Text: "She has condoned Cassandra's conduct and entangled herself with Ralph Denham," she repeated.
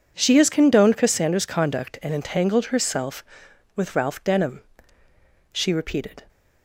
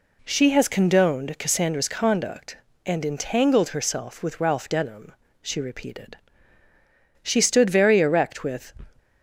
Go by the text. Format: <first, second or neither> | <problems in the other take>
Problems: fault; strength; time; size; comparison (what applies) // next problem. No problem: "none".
first | goes on to say "She stood very erect with"; from 7.2 s on; 1.5 s long